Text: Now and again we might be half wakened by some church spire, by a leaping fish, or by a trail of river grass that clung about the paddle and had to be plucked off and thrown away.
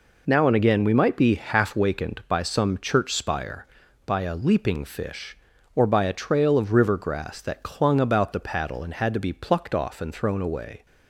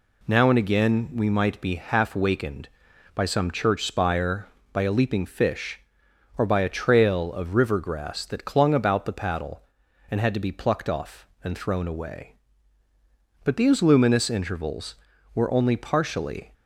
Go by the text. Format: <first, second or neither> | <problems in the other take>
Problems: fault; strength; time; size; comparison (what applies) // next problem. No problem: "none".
first | goes on to say "But these luminous intervals were only partially"; strong; from 13.4 s on; 3.0 s long